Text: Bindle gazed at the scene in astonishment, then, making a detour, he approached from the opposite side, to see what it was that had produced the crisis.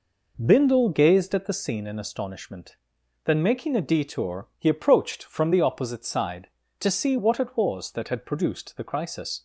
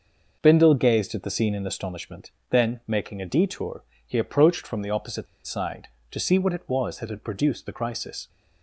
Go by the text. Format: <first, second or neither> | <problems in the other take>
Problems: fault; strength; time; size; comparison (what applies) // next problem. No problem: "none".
first | pauses between "opposite" and "side"; slight; at 5.2 s; 0.19 s long